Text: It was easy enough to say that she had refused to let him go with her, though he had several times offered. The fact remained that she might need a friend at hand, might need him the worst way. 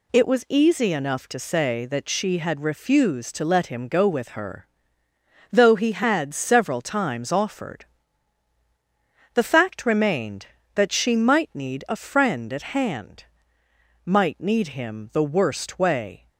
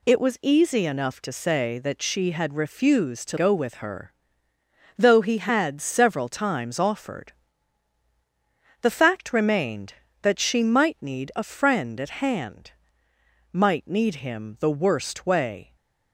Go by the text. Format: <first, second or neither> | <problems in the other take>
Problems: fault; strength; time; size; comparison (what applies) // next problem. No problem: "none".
first | skips "let him"; at 3.3 s // stays silent after the last word; slight; from 15.6 s on; 0.5 s long